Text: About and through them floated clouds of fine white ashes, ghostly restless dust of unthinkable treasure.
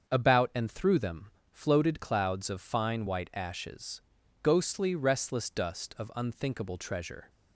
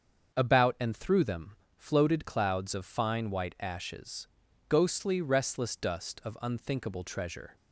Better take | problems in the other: neither | starts louder than the rest; the same in both // pauses between "them" and "floated"; slight; the same in both

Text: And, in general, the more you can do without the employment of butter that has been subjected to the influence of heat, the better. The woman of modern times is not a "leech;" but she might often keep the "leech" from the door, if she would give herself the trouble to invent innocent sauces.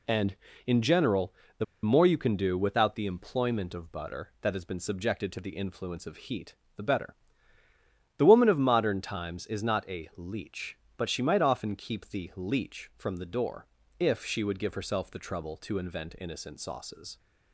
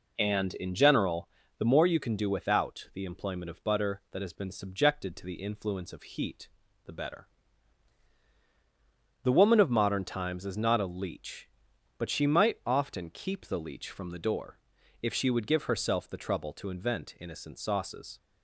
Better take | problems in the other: second | pauses between "the" and "more"; slight; at 1.6 s; 0.19 s long

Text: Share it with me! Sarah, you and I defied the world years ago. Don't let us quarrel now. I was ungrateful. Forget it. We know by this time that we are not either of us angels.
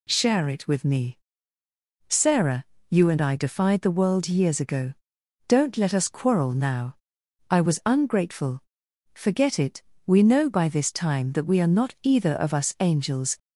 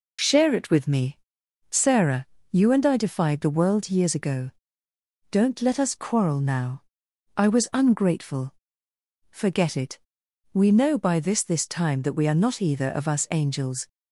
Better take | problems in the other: first | says "this" twice; at 11.4 s

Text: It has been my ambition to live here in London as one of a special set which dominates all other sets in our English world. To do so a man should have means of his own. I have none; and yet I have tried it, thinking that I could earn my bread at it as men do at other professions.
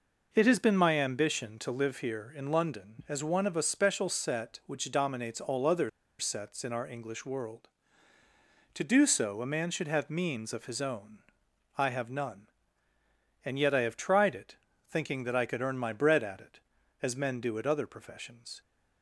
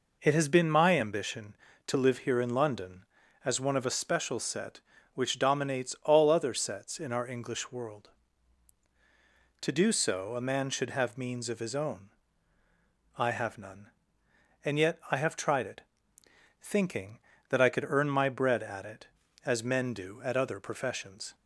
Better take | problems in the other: second | pauses between "other" and "sets"; slight; at 5.8 s; 0.29 s long

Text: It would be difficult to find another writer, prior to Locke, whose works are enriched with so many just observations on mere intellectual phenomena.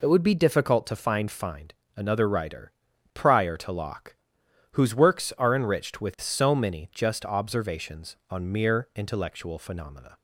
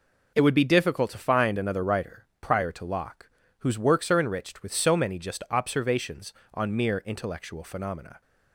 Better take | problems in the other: second | says "find" twice; at 1.2 s

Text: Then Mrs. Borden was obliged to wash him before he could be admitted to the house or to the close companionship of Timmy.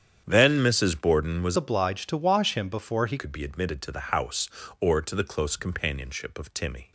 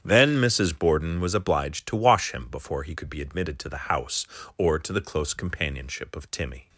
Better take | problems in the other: second | starts louder than the rest; strong; until 1.2 s; 8.5 dB; strong in the second // changes voice from "obliged" to "he"; from 1.5 to 3.1 s; 1.6 s long

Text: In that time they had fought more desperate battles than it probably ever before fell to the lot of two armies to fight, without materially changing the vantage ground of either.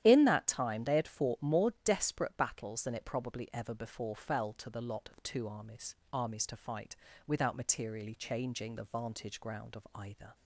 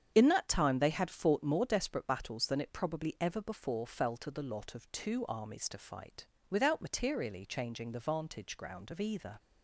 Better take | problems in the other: second | starts louder than the rest; strong; until 1.0 s; 11 dB; strong in the second // says "armies" twice; at 6.1 s

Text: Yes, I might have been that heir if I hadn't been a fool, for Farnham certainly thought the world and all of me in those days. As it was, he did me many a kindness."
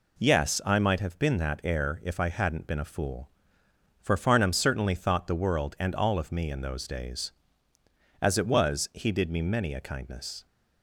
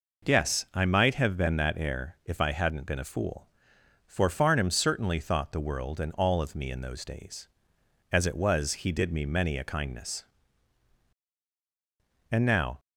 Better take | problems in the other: first | goes on to say "And now"; slight; from 12.3 s on; 0.48 s long

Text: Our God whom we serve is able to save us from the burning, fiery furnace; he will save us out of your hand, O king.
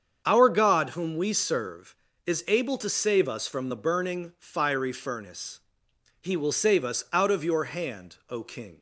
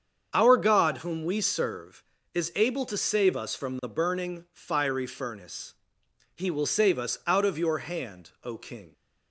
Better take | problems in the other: neither | starts louder than the rest; strong; the same in both

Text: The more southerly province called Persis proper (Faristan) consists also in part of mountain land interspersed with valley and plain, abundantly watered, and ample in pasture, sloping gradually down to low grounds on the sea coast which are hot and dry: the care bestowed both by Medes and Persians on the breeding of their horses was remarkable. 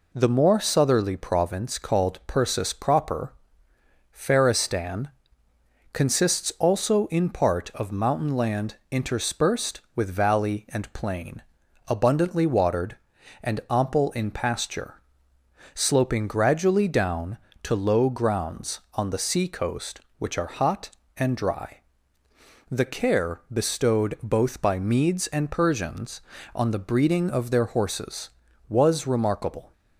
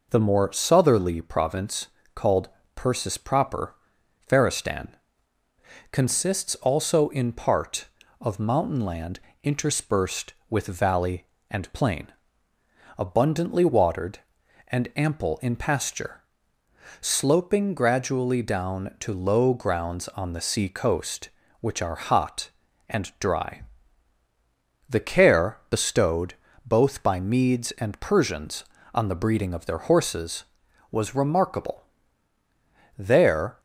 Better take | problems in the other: first | pauses between "province" and "called"; slight; at 1.8 s; 0.28 s long // pauses between "called" and "Persis"; slight; at 2.4 s; 0.26 s long // pauses between "land" and "interspersed"; slight; at 9.1 s; 0.24 s long // pauses between "bestowed" and "both"; slight; at 26.3 s; 0.32 s long // goes on to say "There"; noticeable; from 32.9 s on; 0.62 s long

